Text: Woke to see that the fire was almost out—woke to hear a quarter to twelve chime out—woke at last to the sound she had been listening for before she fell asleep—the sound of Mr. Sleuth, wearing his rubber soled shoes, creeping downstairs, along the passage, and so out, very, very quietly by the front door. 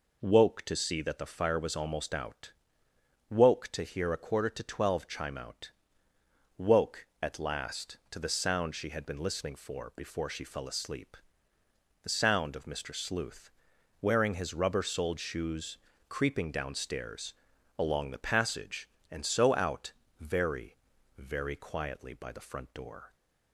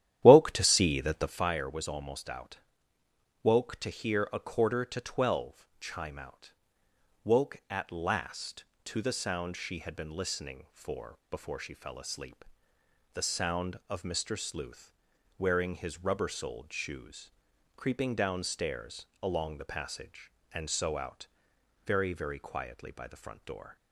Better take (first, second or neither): first